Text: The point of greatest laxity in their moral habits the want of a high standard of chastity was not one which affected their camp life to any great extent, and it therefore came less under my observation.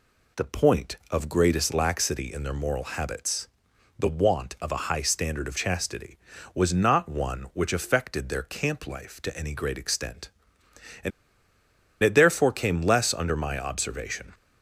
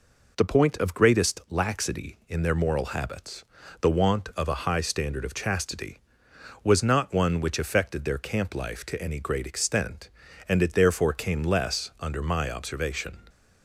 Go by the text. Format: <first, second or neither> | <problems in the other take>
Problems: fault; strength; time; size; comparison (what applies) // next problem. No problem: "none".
second | pauses between "habits" and "the"; noticeable; at 3.4 s; 0.52 s long; slight in the second // pauses between "and" and "it"; noticeable; at 11.1 s; 0.92 s long